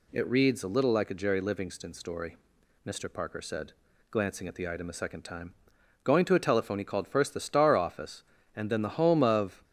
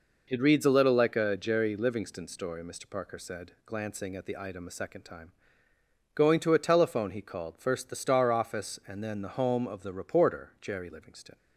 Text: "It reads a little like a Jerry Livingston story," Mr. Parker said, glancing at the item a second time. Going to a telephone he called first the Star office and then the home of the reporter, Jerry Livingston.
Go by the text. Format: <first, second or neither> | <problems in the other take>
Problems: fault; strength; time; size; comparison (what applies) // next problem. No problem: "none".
second | stops before "the reporter Jerry Livingston"; at 9.6 s